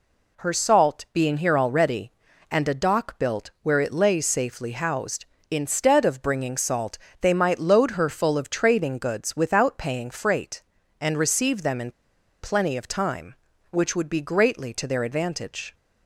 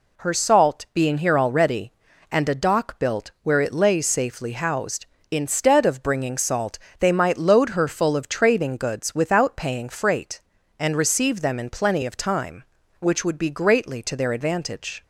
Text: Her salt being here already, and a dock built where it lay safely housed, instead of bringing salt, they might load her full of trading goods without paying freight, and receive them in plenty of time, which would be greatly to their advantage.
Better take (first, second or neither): second